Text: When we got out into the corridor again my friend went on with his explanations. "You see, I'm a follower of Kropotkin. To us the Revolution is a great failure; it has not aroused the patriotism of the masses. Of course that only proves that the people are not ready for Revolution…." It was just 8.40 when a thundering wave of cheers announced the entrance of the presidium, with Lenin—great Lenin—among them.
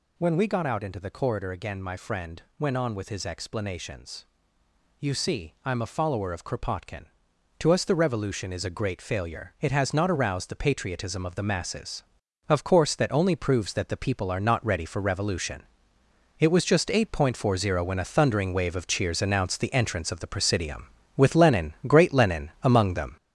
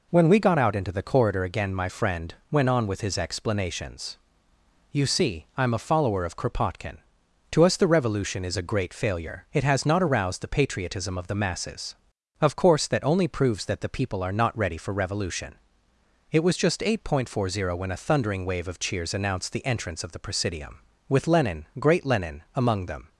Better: second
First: gets louder; throughout; 6.5 dB // pauses between "friend" and "went"; slight; at 2.4 s; 0.18 s long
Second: pauses between "friend" and "went"; slight; at 2.3 s; 0.18 s long

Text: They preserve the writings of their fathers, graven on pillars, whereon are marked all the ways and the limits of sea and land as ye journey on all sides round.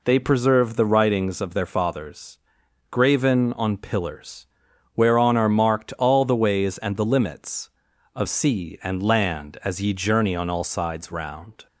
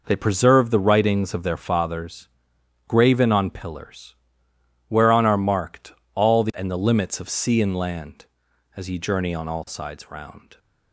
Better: first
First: none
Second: pauses between "marked" and "all"; slight; at 5.9 s; 0.20 s long // skips "ways"; at 6.5 s

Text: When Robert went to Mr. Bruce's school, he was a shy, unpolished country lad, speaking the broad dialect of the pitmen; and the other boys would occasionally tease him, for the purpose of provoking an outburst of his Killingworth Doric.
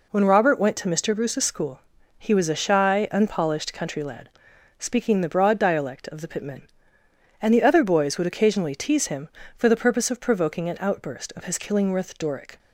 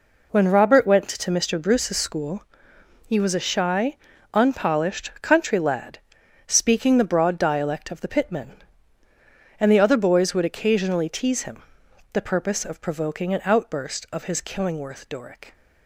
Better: first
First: none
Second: skips "for"; at 11.8 s

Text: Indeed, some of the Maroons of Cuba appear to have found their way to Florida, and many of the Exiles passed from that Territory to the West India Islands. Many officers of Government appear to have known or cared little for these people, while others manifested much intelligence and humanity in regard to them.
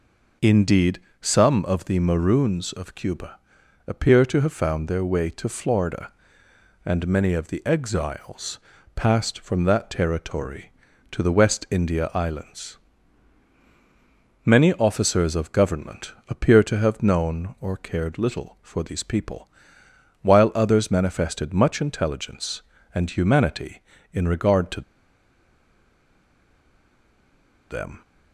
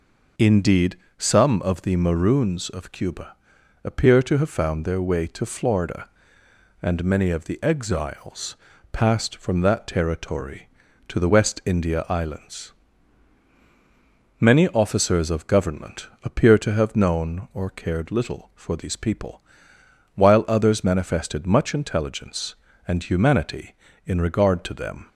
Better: second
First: pauses between "Cuba" and "appear"; noticeable; at 3.3 s; 0.48 s long // pauses between "Exiles" and "passed"; slight; at 8.5 s; 0.36 s long // pauses between "Government" and "appear"; slight; at 16.1 s; 0.16 s long // pauses between "to" and "them"; strong; at 24.8 s; 2.8 s long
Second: pauses between "Cuba" and "appear"; noticeable; at 3.3 s; 0.48 s long // pauses between "Exiles" and "passed"; slight; at 8.5 s; 0.36 s long // pauses between "Government" and "appear"; slight; at 16.0 s; 0.16 s long

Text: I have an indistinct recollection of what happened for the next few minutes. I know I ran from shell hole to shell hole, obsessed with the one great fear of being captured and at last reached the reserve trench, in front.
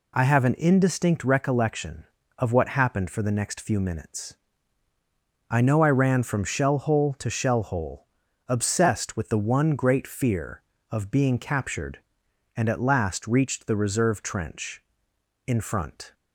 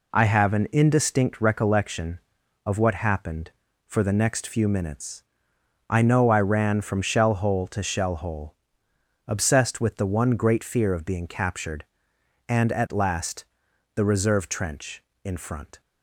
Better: first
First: none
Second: skips "reached"; at 13.6 s

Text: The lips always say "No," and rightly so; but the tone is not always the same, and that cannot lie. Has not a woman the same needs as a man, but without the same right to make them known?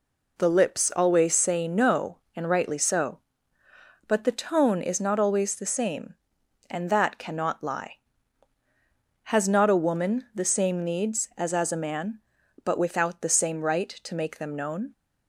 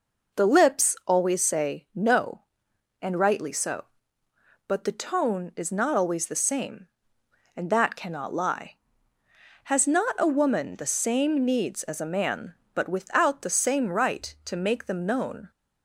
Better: second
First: says "as" twice; at 11.5 s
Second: none

